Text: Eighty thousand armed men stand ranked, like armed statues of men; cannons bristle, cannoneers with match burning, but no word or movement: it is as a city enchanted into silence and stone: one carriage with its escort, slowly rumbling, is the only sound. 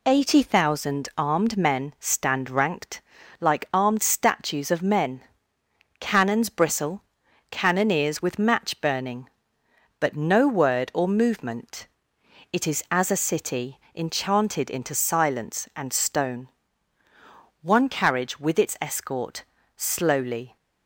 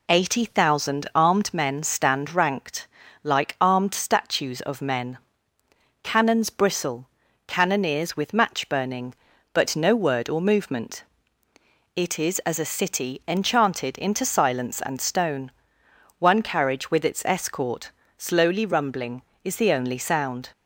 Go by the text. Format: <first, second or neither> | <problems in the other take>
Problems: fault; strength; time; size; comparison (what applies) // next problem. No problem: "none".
second | pauses between "city" and "enchanted"; slight; at 13.7 s; 0.16 s long // stops before "rumbling is the only sound"; at 20.5 s